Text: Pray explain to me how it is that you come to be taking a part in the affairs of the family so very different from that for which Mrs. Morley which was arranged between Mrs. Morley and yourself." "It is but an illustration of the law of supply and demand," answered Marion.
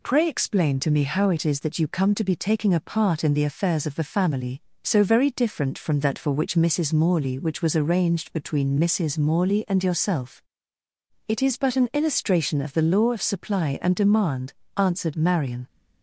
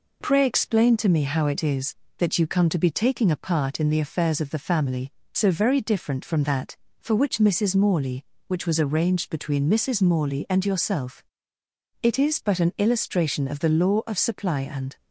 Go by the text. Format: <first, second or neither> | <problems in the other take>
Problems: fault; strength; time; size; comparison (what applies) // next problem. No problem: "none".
first | stops before "demand answered Marion"; at 14.9 s